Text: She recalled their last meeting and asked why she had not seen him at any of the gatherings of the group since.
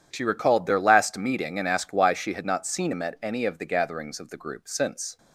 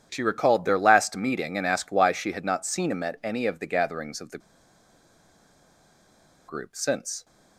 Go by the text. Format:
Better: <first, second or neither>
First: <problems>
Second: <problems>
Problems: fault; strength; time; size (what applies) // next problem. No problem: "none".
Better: first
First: none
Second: pauses between "the" and "group"; strong; at 4.3 s; 2.0 s long